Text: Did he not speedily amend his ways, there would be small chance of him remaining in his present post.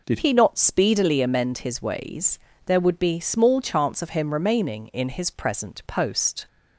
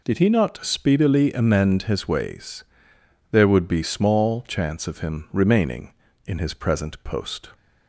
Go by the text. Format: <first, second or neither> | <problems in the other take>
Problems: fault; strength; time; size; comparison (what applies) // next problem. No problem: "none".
second | changes voice at "he"; from 0.1 s on; 6.3 s long